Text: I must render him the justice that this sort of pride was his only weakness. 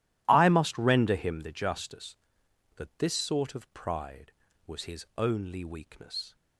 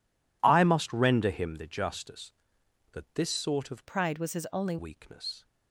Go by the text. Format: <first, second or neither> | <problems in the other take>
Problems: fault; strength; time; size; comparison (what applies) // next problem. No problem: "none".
first | changes voice from "pride" to "only"; from 3.8 to 4.7 s; 0.9 s long